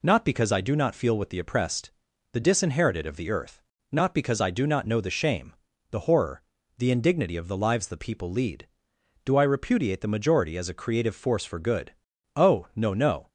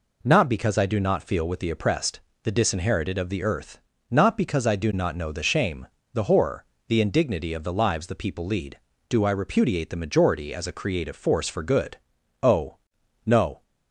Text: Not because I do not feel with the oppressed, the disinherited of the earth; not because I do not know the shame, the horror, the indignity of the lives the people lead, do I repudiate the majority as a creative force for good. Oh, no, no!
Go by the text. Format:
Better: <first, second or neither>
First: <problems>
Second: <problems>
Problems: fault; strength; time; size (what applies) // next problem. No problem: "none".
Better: first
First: none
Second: stops before "no"; at 13.6 s